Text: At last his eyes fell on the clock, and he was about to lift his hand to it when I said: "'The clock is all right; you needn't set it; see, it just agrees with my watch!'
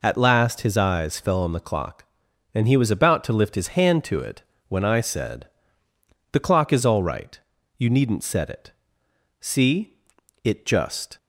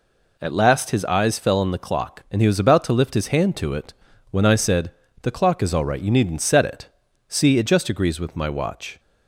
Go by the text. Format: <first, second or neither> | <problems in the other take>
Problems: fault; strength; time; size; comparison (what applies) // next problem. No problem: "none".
second | pauses between "it" and "when"; slight; at 4.4 s; 0.26 s long; slight in the second // stops before "agrees with my watch"; at 11.1 s